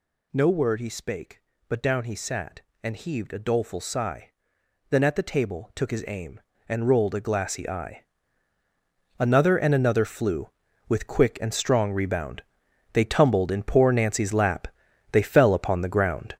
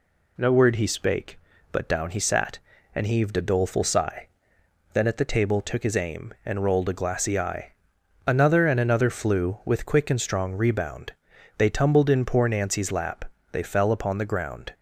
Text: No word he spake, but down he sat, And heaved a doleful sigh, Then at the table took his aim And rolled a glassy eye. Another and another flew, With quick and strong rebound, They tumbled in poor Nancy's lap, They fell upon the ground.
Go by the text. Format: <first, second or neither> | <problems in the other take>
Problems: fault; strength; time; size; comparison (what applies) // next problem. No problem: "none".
second | gets louder; strong; throughout; 8.5 dB